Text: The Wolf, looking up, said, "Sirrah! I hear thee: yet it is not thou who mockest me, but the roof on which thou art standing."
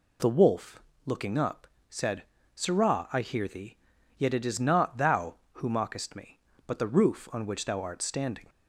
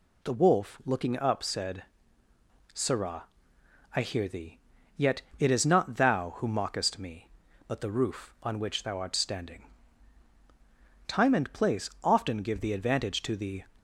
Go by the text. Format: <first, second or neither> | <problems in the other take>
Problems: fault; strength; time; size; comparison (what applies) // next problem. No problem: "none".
first | pauses between "yet" and "it"; slight; at 5.2 s; 0.18 s long // goes on to say "Time and place often give the advantage to the"; strong; from 11.0 s on; 2.5 s long